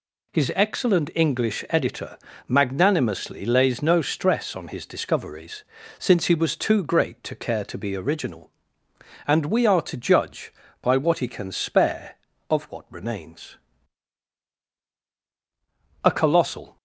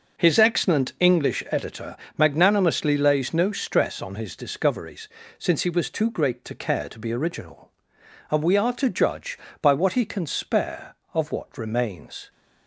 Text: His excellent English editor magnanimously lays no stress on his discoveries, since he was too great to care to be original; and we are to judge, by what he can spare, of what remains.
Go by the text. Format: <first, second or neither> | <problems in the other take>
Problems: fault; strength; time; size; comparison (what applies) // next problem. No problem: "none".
second | pauses between "editor" and "magnanimously"; slight; at 2.1 s; 0.28 s long; slight in the second // goes on to say "A colossal"; noticeable; from 16.0 s on; 0.72 s long